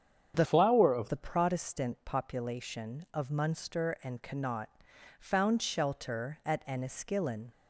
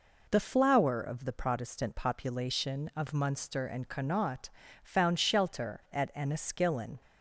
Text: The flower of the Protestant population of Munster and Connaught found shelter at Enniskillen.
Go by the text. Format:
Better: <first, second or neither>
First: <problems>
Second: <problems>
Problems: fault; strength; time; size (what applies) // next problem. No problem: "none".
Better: second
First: starts louder than the rest; strong; until 1.3 s; 7.5 dB // changes voice from "flower" to "of"; from 0.4 to 1.0 s; 0.6 s long // pauses between "Connaught" and "found"; noticeable; at 4.6 s; 0.50 s long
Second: pauses between "Connaught" and "found"; slight; at 4.5 s; 0.32 s long